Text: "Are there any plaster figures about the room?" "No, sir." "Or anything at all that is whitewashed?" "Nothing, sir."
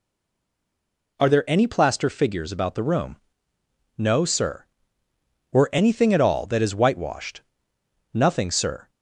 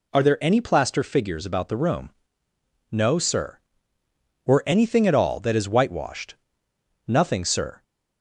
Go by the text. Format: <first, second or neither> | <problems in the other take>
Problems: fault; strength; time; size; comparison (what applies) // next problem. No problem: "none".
second | stays silent before the first word; noticeable; until 1.1 s; 1.1 s long